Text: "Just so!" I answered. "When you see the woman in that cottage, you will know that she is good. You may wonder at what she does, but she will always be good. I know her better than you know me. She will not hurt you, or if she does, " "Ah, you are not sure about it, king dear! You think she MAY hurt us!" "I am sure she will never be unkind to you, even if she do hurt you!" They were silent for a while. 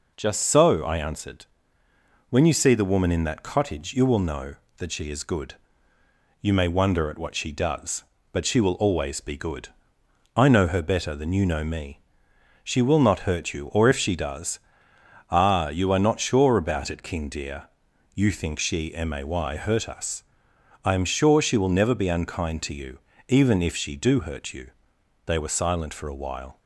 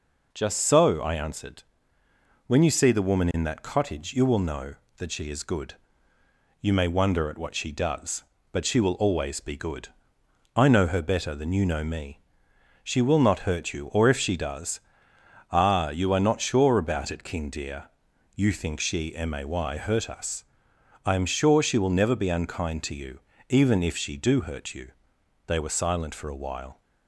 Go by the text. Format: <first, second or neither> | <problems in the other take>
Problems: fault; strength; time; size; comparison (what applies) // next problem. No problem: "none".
neither | none